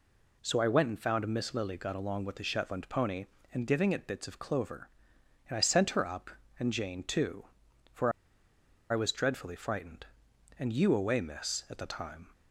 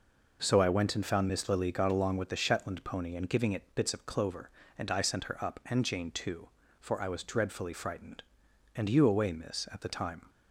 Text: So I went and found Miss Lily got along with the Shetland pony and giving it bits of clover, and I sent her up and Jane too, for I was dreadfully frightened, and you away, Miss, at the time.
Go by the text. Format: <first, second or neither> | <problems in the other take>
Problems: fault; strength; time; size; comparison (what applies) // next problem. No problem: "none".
second | pauses between "for" and "I"; noticeable; at 8.0 s; 0.81 s long